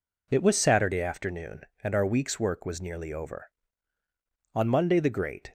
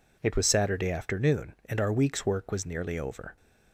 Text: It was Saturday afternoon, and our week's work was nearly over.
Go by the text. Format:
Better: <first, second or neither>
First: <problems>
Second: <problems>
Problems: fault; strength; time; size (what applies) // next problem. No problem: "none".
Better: second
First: goes on to say "On Monday the great"; noticeable; from 4.5 s on; 0.98 s long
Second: none